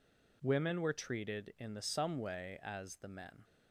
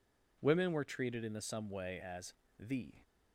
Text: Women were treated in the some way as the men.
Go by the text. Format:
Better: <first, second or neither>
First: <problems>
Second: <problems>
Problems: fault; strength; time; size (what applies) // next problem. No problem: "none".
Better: first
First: none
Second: pauses between "as" and "the"; slight; at 2.3 s; 0.26 s long // stops before "men"; at 3.0 s